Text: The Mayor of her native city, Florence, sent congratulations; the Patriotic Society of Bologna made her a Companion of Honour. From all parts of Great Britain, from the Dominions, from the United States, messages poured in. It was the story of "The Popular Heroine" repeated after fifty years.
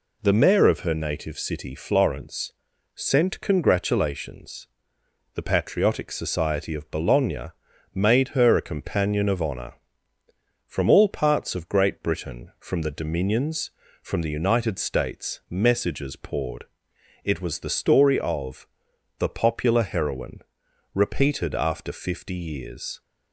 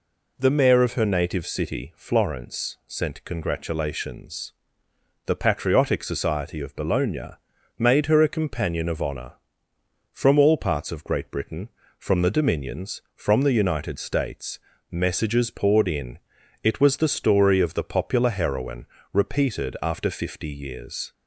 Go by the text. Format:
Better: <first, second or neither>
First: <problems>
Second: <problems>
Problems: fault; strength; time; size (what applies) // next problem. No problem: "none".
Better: second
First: pauses between "Bologna" and "made"; at 7.5 s; 0.42 s long // skips "in"; at 16.9 s // pauses between "of" and "The"; noticeable; at 18.6 s; 0.54 s long // pauses between "Heroine" and "repeated"; noticeable; at 20.4 s; 0.54 s long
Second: pauses between "Bologna" and "made"; at 7.3 s; 0.42 s long // pauses between "Heroine" and "repeated"; slight; at 18.8 s; 0.26 s long